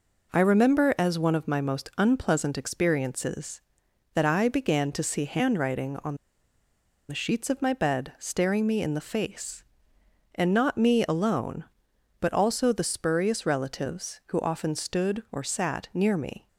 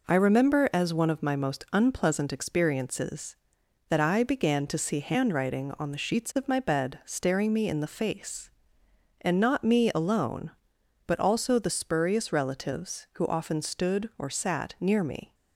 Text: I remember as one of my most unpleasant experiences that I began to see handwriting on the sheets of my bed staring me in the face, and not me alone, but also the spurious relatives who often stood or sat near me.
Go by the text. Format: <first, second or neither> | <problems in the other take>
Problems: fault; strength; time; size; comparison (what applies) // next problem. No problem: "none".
second | pauses between "on" and "the"; noticeable; at 6.1 s; 0.93 s long